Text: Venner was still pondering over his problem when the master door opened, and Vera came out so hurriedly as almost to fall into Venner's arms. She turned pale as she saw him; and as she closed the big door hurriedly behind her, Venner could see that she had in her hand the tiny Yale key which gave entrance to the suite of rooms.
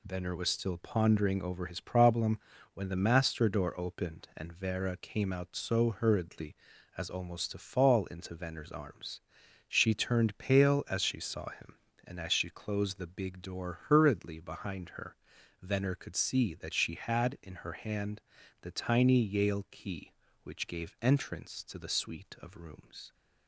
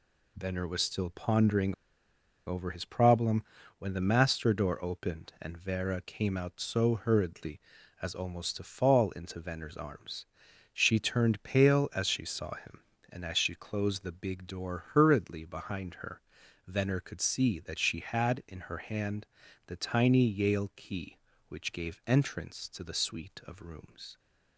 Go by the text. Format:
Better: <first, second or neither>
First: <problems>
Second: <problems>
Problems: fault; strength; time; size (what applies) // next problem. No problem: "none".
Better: first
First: pauses between "problem" and "when"; slight; at 2.3 s; 0.34 s long // pauses between "hand" and "the"; at 18.2 s; 0.42 s long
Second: pauses between "pondering" and "over"; noticeable; at 1.7 s; 0.72 s long // pauses between "problem" and "when"; slight; at 3.4 s; 0.34 s long // pauses between "hand" and "the"; at 19.2 s; 0.42 s long